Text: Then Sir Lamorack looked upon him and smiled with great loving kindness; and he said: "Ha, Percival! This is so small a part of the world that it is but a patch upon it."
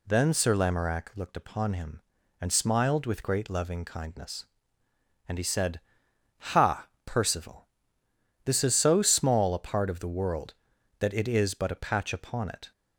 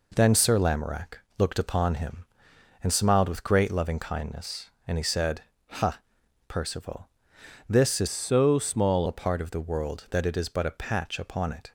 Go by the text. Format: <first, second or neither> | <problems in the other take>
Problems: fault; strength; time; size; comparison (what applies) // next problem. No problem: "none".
first | pauses between "Lamorack" and "looked"; slight; at 1.1 s; 0.20 s long // changes voice from "so" to "small"; from 8.0 to 9.0 s; 1.0 s long